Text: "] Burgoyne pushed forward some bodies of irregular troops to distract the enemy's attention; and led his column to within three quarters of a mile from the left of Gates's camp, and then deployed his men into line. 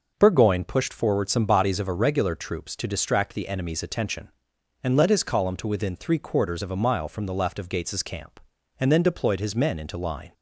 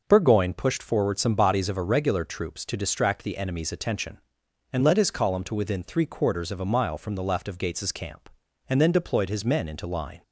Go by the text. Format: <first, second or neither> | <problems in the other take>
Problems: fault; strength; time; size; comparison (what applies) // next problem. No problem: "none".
neither | none